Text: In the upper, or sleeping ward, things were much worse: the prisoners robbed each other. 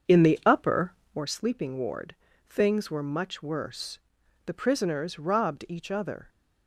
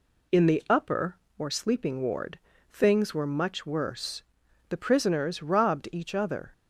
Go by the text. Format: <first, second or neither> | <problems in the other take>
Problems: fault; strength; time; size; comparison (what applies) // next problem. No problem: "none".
second | starts louder than the rest; until 1.4 s; 6.5 dB